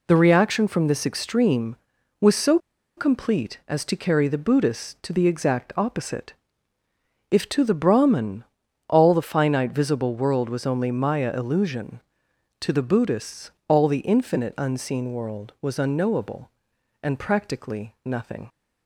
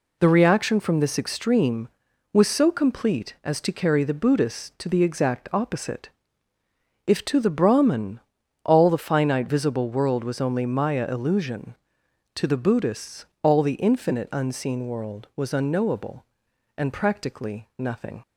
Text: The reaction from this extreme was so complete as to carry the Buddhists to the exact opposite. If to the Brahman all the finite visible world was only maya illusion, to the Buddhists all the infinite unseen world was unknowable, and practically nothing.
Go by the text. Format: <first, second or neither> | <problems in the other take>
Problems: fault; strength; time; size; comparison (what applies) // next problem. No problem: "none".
second | pauses between "so" and "complete"; at 2.5 s; 0.39 s long // pauses between "Brahman" and "all"; at 8.4 s; 0.44 s long; also in the second // pauses between "Buddhists" and "all"; slight; at 13.5 s; 0.16 s long; slight in the second